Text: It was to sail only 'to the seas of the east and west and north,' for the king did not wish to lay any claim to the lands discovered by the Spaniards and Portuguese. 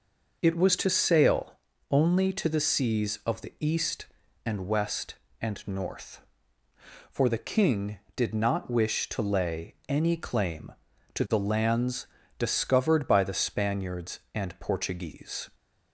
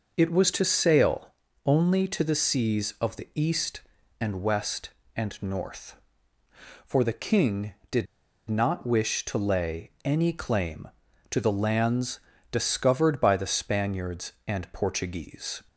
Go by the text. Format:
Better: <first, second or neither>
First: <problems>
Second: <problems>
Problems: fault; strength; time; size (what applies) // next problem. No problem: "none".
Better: first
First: pauses between "sail" and "only"; slight; at 1.5 s; 0.34 s long // pauses between "lands" and "discovered"; slight; at 12.0 s; 0.32 s long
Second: pauses between "sail" and "only"; slight; at 1.3 s; 0.34 s long // pauses between "did" and "not"; at 8.0 s; 0.43 s long // pauses between "lands" and "discovered"; slight; at 12.1 s; 0.32 s long